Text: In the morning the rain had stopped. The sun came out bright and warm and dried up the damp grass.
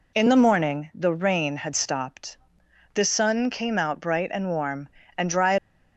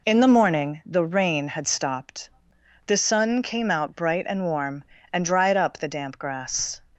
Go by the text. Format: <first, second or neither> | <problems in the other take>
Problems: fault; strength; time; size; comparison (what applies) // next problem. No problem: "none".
second | stops before "up the damp grass"; at 5.5 s